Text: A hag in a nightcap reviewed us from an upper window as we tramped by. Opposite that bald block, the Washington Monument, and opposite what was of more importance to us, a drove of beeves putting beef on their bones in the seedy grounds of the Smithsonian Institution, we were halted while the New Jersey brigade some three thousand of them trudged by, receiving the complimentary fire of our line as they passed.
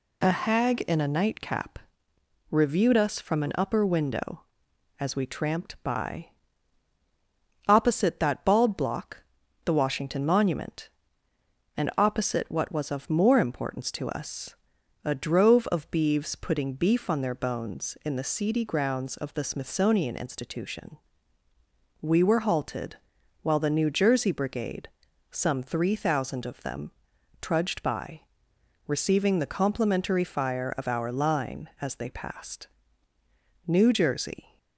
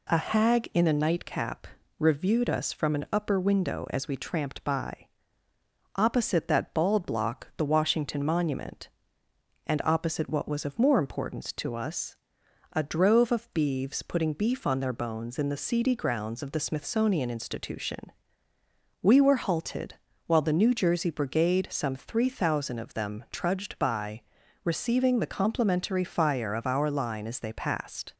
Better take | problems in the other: second | pauses between "nightcap" and "reviewed"; noticeable; at 1.8 s; 0.72 s long; slight in the second // pauses between "halted" and "while"; noticeable; at 22.9 s; 0.48 s long; slight in the second // pauses between "brigade" and "some"; noticeable; at 24.8 s; 0.46 s long // pauses between "them" and "trudged"; noticeable; at 26.9 s; 0.48 s long // goes on to say "New Jersey"; noticeable; from 33.6 s on; 0.93 s long

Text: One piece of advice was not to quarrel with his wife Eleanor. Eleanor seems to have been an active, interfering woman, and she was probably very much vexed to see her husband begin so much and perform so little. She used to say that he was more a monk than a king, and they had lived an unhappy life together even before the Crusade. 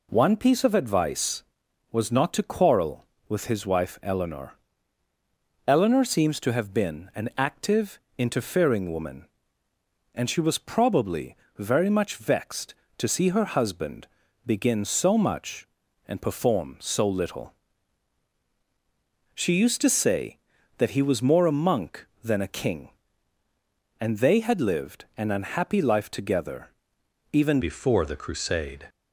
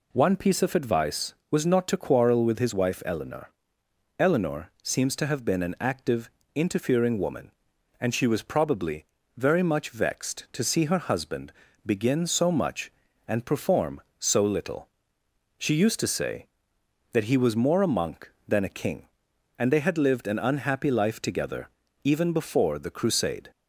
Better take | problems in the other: second | pauses between "probably" and "very"; slight; at 11.3 s; 0.24 s long; slight in the second // pauses between "husband" and "begin"; at 14.0 s; 0.40 s long; slight in the second // pauses between "together" and "even"; noticeable; at 26.6 s; 0.62 s long; slight in the second // changes voice at "before"; from 27.6 s on; 1.2 s long

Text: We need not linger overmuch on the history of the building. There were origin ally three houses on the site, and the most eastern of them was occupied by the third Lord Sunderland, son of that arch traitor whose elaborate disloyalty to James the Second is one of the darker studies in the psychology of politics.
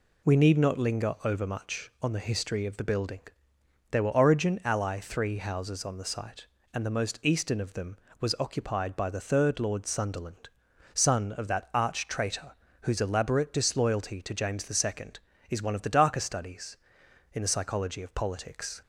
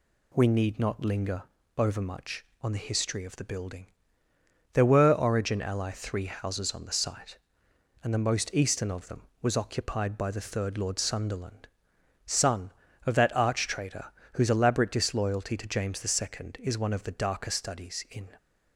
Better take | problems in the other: first | pauses between "linger" and "overmuch"; slight; at 1.4 s; 0.34 s long // pauses between "traitor" and "whose"; slight; at 14.0 s; 0.26 s long; slight in the first // stops before "the psychology of politics"; at 18.3 s

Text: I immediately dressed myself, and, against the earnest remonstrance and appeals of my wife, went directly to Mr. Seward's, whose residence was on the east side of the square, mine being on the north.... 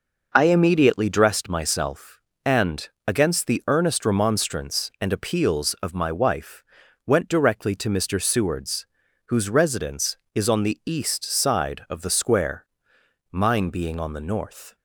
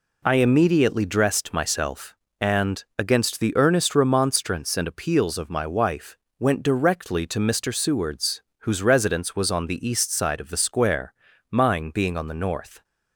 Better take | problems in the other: second | says "is" for "was"; at 10.3 s

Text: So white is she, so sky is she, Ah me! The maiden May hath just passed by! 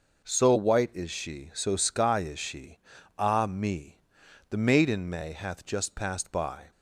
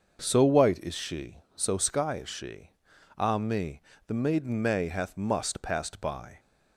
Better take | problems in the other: first | starts louder than the rest; until 1.2 s; 6.5 dB // says "must" for "just"; at 5.1 s

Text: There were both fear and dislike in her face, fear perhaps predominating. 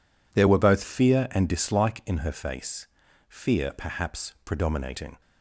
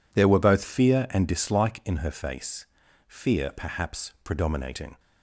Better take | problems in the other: neither | none

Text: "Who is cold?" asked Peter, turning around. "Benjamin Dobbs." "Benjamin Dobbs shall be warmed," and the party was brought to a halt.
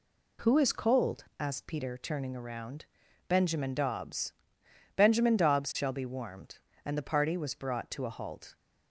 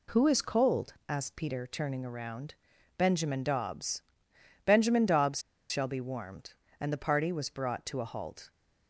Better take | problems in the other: first | pauses between "Dobbs" and "shall"; slight; at 5.4 s; 0.29 s long

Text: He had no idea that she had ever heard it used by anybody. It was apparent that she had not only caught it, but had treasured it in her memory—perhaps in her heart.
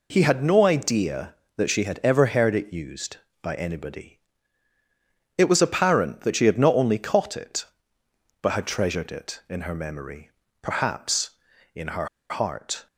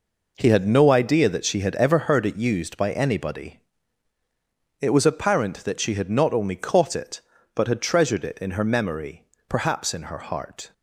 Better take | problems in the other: second | pauses between "her" and "heart"; slight; at 12.0 s; 0.22 s long

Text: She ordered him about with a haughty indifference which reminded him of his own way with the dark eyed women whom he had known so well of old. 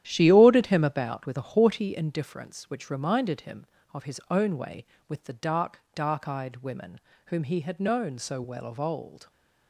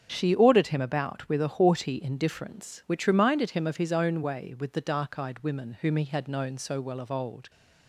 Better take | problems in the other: second | starts louder than the rest; strong; until 1.0 s; 11 dB; also in the second // says "dark" twice; at 5.9 s // pauses between "women" and "whom"; slight; at 7.0 s; 0.28 s long

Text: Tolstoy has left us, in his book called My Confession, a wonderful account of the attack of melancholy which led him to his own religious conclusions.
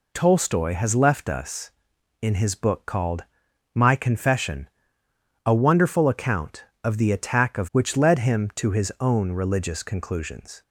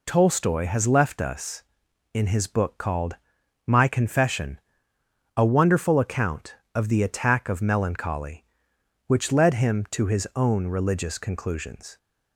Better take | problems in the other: second | pauses between "called" and "My"; noticeable; at 3.2 s; 0.50 s long; noticeable in the second // skips "melancholy"; at 7.7 s

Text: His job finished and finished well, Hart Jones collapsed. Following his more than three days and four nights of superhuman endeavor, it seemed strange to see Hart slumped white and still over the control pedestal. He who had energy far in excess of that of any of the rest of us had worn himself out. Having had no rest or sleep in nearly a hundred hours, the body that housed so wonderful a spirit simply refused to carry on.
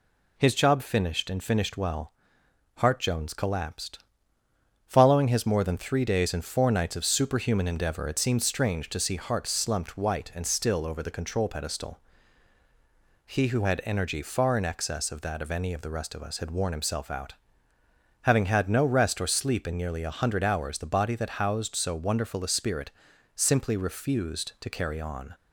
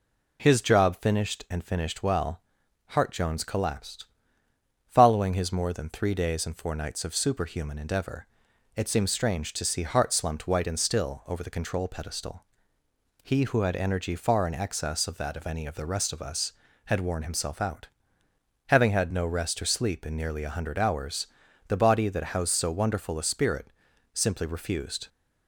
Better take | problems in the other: first | pauses between "spirit" and "simply"; noticeable; at 23.6 s; 0.48 s long; noticeable in the first // stops before "to carry on"; at 25.0 s

